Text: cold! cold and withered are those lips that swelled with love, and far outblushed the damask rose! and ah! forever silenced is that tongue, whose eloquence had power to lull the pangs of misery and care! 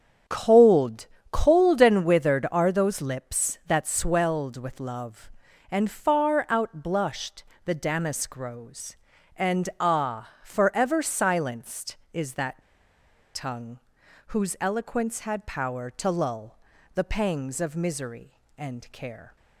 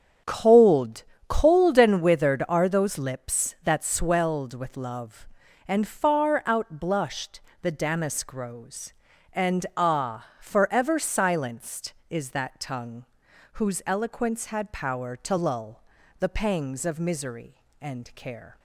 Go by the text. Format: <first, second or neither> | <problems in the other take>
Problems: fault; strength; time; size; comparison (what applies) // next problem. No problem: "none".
second | starts louder than the rest; strong; until 1.5 s; 8 dB; strong in the second // pauses between "outblushed" and "the"; slight; at 7.4 s; 0.22 s long; slight in the second // pauses between "that" and "tongue"; noticeable; at 12.6 s; 0.74 s long // pauses between "lull" and "the"; at 16.5 s; 0.38 s long; also in the second